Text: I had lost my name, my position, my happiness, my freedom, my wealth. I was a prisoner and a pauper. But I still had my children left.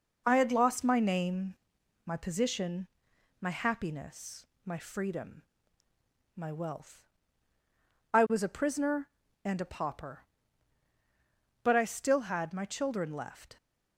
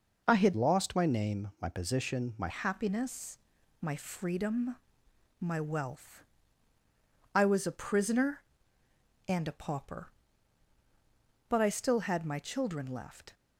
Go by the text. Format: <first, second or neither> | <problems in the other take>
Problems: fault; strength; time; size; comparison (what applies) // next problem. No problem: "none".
first | changes voice from "lost" to "my"; from 0.5 to 2.4 s; 1.9 s long